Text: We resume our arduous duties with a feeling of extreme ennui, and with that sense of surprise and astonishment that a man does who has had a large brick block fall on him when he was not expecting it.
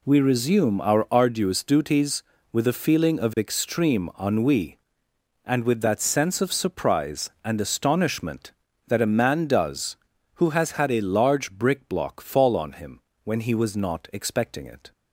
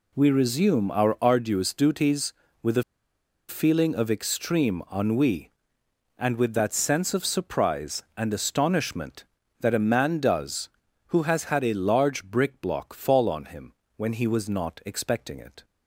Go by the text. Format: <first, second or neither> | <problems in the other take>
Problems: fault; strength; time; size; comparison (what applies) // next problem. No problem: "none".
first | pauses between "a" and "feeling"; noticeable; at 2.8 s; 0.66 s long // pauses between "him" and "when"; slight; at 13.7 s; 0.24 s long; slight in the first